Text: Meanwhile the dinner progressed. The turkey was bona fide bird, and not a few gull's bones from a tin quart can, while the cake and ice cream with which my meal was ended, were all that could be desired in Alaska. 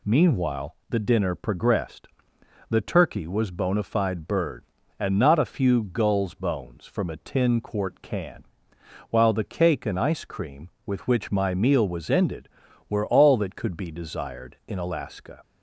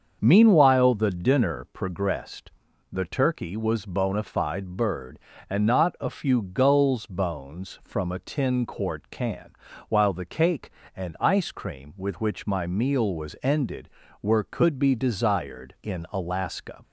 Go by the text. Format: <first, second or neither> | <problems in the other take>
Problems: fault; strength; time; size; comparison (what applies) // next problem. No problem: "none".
first | starts louder than the rest; until 1.2 s; 6.5 dB // skips "all that"; at 14.4 s